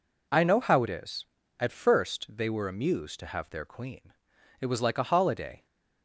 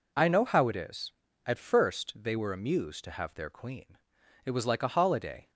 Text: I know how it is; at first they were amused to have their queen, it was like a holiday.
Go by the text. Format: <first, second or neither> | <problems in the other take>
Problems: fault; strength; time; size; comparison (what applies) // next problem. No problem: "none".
neither | none